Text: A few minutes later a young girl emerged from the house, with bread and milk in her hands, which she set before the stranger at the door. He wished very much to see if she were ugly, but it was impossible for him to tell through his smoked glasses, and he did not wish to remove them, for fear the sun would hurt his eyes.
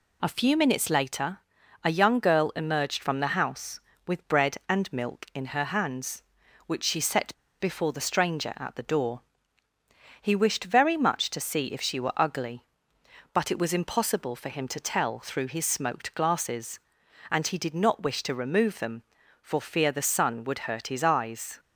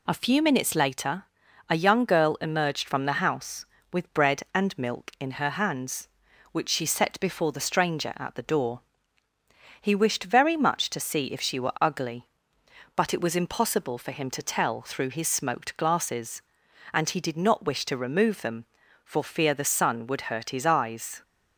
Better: second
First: pauses between "later" and "a"; at 1.3 s; 0.44 s long // pauses between "set" and "before"; slight; at 7.3 s; 0.26 s long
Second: pauses between "later" and "a"; at 1.2 s; 0.44 s long

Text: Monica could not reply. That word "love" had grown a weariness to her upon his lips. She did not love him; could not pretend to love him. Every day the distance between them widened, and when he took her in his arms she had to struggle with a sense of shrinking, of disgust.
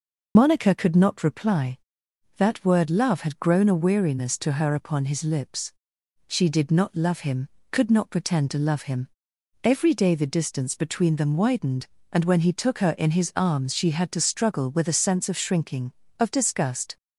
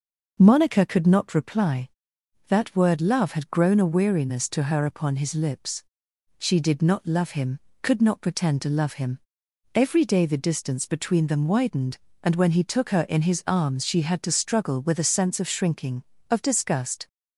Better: second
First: loses the start of "Monica"; at 0.3 s; 65 ms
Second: none

